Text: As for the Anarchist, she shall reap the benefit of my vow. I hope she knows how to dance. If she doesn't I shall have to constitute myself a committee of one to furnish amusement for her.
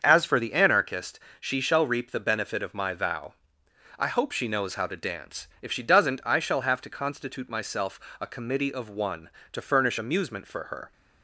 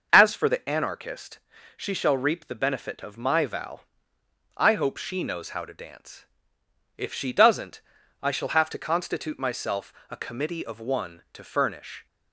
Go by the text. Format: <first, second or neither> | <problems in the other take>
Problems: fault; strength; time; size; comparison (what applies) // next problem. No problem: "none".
first | starts louder than the rest; until 1.1 s; 6 dB; also in the first // pauses between "doesn't" and "I"; at 7.8 s; 0.40 s long // pauses between "myself" and "a"; slight; at 9.9 s; 0.16 s long; slight in the first // stops before "amusement for her"; at 12.0 s